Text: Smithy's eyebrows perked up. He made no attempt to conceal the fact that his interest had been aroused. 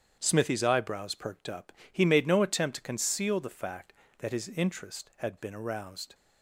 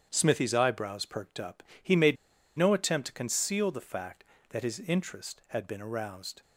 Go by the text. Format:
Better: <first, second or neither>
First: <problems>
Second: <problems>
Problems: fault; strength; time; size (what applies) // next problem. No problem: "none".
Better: first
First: starts louder than the rest; strong; until 1.2 s; 9 dB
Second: starts louder than the rest; strong; until 1.1 s; 9 dB // pauses between "made" and "no"; at 2.1 s; 0.41 s long